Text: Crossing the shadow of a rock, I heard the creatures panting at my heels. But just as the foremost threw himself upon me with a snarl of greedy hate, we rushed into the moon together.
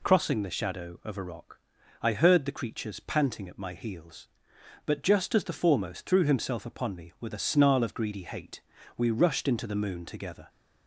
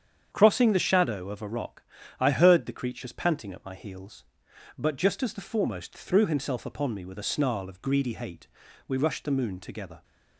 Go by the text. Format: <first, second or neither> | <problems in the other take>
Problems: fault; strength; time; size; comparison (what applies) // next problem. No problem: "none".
first | starts louder than the rest; strong; until 1.3 s; 8 dB // skips "into"; at 9.2 s